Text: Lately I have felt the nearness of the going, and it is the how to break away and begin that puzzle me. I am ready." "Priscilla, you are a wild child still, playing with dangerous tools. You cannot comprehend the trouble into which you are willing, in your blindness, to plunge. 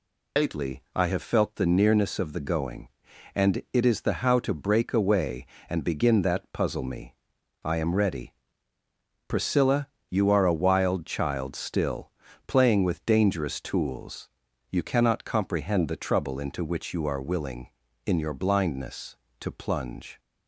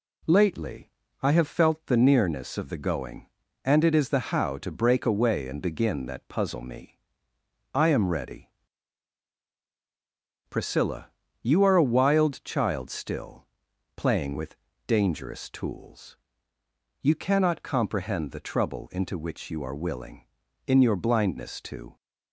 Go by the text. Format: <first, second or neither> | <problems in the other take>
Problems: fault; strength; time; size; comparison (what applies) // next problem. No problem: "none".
first | pauses between "Lately" and "I"; slight; at 0.8 s; 0.32 s long // pauses between "with" and "dangerous"; slight; at 14.5 s; 0.32 s long // stops before "plunge"; at 21.9 s